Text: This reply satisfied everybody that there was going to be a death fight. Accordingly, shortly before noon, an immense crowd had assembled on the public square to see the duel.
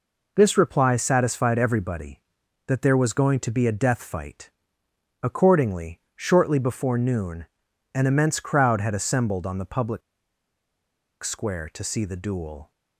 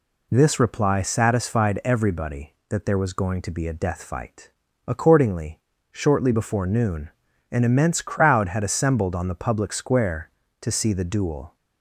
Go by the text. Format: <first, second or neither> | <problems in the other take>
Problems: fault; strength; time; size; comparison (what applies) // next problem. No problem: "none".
second | pauses between "public" and "square"; at 10.0 s; 1.2 s long